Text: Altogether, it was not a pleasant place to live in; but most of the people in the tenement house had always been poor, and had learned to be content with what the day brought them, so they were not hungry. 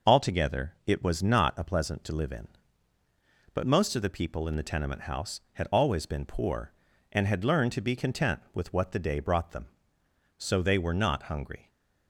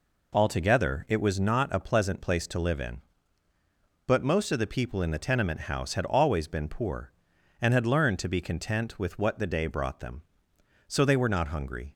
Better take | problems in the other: second | skips "place"; at 2.0 s

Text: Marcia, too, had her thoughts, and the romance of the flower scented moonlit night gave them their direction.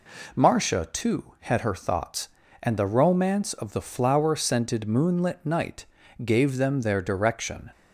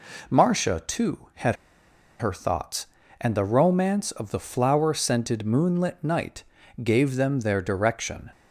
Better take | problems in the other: first | pauses between "had" and "her"; noticeable; at 1.5 s; 0.64 s long // pauses between "night" and "gave"; at 6.4 s; 0.38 s long; also in the first

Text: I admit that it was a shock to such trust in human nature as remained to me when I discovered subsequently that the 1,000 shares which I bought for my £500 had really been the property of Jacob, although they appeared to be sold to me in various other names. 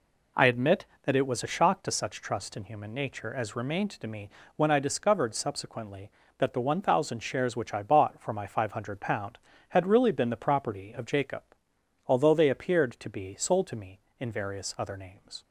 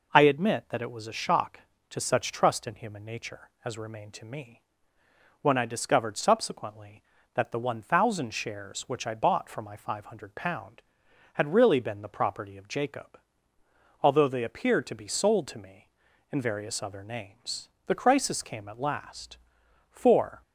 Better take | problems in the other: first | pauses between "me" and "when"; noticeable; at 4.6 s; 0.80 s long; slight in the first // goes on to say "The crisis came at last for"; strong; from 17.8 s on; 2.5 s long

